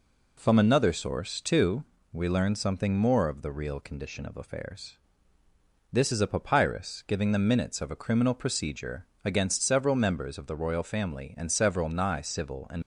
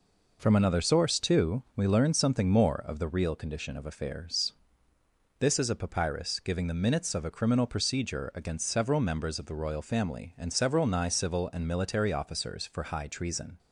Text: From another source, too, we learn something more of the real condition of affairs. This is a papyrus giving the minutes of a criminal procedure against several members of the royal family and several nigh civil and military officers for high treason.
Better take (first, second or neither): second